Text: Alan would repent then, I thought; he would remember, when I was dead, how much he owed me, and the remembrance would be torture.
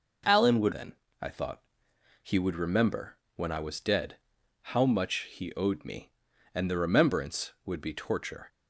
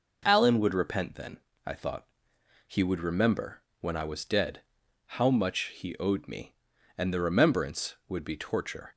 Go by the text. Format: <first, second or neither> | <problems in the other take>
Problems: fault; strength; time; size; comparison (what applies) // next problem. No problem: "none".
second | skips "repent"; at 0.7 s